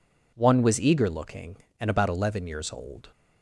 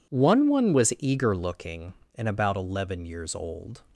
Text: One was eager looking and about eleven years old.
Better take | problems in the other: first | says "One" twice; at 0.4 s

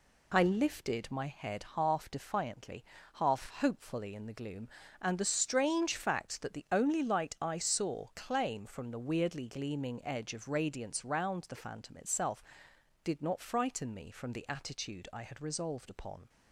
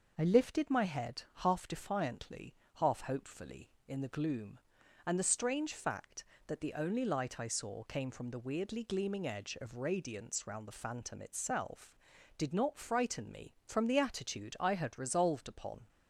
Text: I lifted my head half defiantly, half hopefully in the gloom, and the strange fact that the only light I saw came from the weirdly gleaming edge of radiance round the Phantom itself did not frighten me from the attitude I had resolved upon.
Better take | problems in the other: second | says "claim" for "came"; at 8.1 s

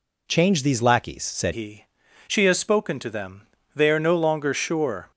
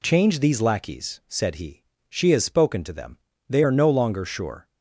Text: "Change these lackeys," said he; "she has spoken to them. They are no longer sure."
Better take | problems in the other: second | changes voice at "he"; from 1.5 s on; 3.6 s long

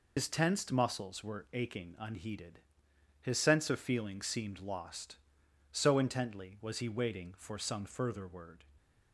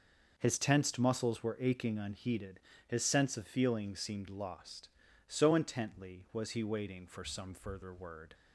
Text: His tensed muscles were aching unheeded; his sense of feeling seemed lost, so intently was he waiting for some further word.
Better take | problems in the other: second | loses the start of "His"; at 0.1 s; 120 ms

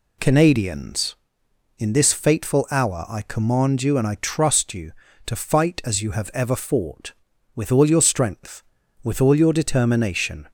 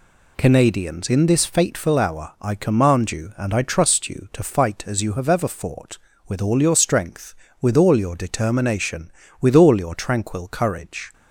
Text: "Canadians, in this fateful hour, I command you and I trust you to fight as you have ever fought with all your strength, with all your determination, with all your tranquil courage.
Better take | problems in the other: second | stops before "with all your tranquil courage"; at 10.4 s

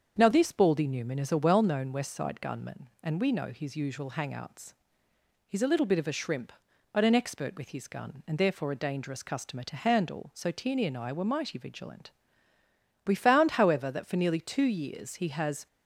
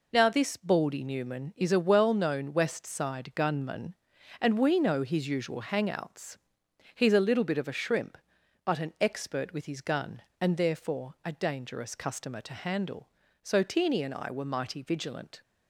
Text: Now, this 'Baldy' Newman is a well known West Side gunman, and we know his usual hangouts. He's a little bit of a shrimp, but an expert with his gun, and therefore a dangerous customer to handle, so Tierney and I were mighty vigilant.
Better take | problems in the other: second | starts louder than the rest; until 1.2 s; 7 dB // goes on to say "We found however that for nearly two years he has"; strong; from 13.0 s on; 2.6 s long

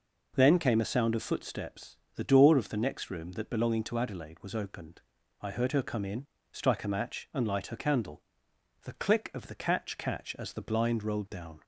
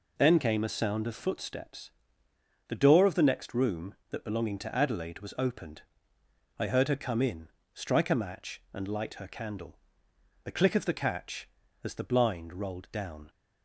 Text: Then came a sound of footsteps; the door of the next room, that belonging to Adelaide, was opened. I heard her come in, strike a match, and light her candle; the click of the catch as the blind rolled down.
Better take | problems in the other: second | says "catch" twice; at 9.9 s

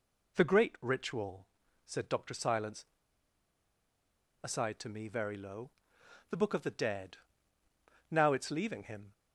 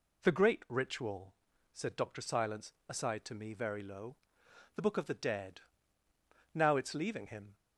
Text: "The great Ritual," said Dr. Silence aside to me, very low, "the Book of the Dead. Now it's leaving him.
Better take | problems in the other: second | pauses between "Silence" and "aside"; strong; at 2.8 s; 1.5 s long

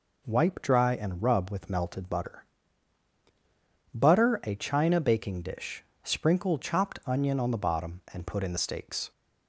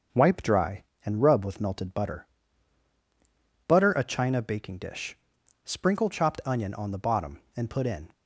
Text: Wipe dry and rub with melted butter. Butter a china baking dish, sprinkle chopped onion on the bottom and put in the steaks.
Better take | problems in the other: first | starts louder than the rest; until 1.3 s; 6.5 dB // stops before "the steaks"; at 8.1 s

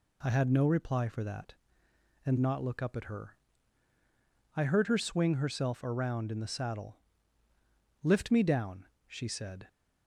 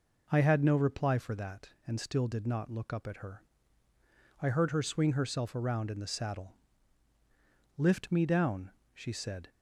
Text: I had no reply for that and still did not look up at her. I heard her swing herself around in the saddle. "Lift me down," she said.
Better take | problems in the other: second | skips "still did"; at 2.3 s

